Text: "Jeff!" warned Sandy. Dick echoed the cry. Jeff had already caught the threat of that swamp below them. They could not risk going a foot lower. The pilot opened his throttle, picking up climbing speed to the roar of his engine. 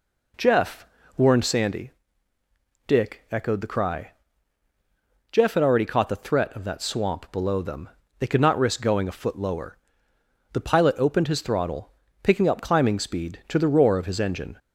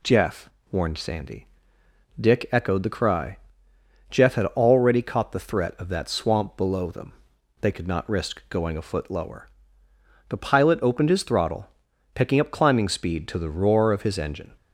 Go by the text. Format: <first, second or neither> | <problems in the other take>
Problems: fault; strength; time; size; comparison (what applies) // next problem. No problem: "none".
neither | none